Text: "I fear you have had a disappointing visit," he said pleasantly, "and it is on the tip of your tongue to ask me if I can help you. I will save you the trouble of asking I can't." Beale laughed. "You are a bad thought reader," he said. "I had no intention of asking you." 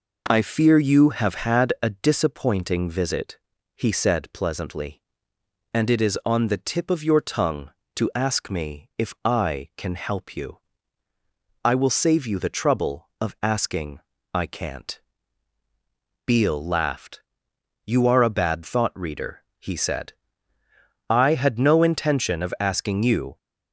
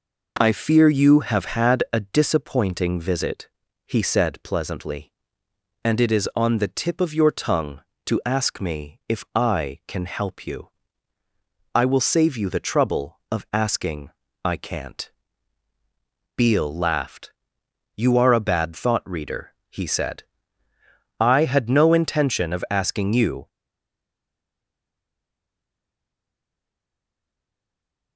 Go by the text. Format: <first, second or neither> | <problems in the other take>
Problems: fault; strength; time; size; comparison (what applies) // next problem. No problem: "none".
first | pauses between "asking" and "I"; slight; at 14.1 s; 0.34 s long; slight in the first // stays silent after the last word; strong; from 23.4 s on; 4.7 s long